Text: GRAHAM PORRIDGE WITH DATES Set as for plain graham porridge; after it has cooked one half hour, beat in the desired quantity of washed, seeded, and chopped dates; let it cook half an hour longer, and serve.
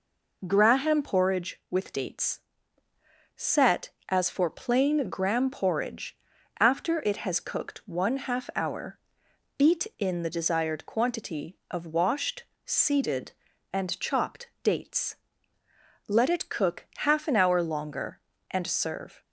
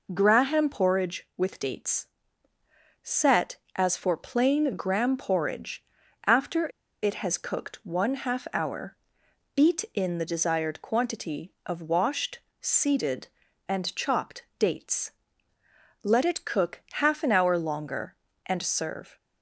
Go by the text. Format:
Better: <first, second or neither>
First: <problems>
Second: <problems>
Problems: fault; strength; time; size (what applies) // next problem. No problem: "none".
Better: first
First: pauses between "DATES" and "Set"; noticeable; at 2.4 s; 0.96 s long // pauses between "chopped" and "dates"; slight; at 14.4 s; 0.16 s long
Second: pauses between "DATES" and "Set"; noticeable; at 2.0 s; 0.96 s long // pauses between "after" and "it"; at 6.6 s; 0.36 s long // pauses between "chopped" and "dates"; slight; at 14.4 s; 0.16 s long